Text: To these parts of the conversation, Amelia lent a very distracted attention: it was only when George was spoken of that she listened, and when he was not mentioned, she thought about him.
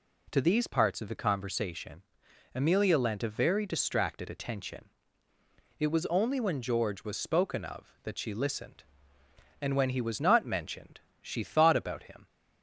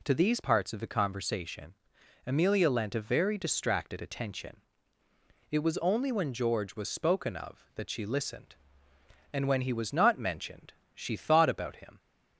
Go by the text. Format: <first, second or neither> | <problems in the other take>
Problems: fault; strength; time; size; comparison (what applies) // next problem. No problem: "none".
neither | none